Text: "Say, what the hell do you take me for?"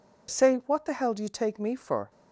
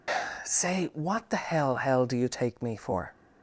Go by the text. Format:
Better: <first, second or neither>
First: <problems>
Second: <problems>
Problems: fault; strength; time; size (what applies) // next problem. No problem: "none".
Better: first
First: none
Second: says "hell" twice; at 1.7 s